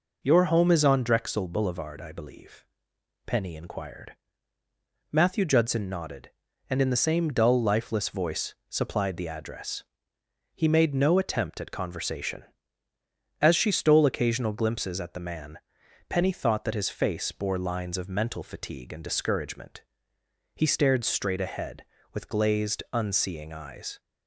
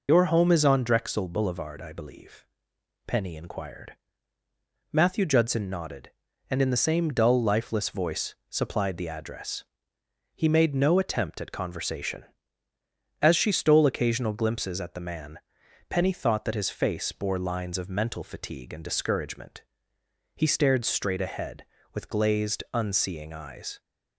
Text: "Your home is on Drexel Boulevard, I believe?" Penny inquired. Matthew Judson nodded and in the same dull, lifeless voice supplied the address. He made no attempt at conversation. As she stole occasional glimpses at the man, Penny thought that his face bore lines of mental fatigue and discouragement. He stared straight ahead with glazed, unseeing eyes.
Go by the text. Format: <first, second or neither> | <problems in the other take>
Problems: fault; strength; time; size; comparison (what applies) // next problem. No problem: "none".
first | loses the start of "Your"; at 0.0 s; 45 ms // pauses between "voice" and "supplied"; slight; at 8.3 s; 0.16 s long; slight in the first